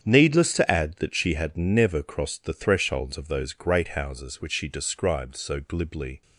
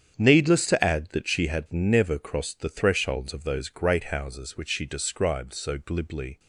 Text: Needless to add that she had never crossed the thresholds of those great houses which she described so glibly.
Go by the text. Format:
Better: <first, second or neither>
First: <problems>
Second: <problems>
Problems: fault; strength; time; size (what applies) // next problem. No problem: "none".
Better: neither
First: starts louder than the rest; strong; until 1.0 s; 8.5 dB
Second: starts louder than the rest; strong; until 1.1 s; 8.5 dB